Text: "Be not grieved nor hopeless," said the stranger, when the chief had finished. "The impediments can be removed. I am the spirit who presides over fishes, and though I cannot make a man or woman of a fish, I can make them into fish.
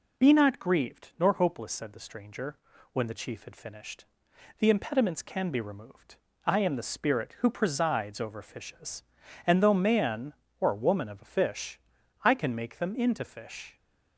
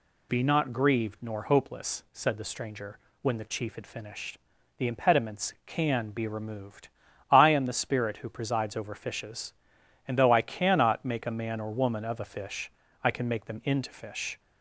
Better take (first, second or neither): second